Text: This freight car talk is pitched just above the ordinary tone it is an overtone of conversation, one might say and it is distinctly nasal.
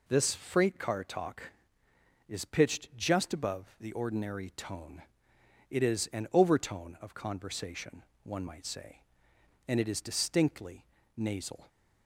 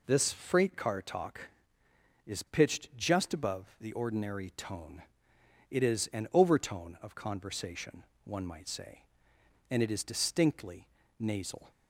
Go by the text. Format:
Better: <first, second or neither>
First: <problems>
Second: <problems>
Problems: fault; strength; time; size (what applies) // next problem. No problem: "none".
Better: neither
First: pauses between "tone" and "it"; noticeable; at 5.0 s; 0.66 s long // pauses between "distinctly" and "nasal"; slight; at 10.8 s; 0.32 s long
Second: pauses between "tone" and "it"; noticeable; at 5.0 s; 0.66 s long // pauses between "distinctly" and "nasal"; slight; at 10.8 s; 0.32 s long